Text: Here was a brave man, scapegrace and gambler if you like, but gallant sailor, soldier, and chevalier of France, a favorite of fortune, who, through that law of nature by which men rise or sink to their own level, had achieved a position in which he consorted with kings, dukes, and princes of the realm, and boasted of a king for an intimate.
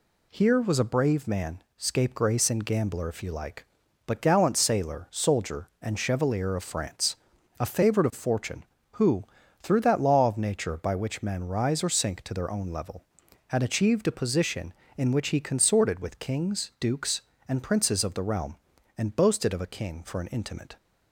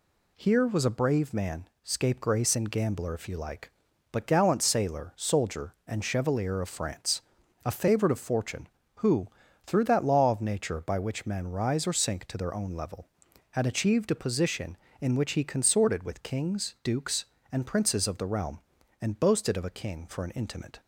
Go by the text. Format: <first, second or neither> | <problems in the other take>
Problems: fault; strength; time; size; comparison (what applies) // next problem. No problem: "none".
neither | none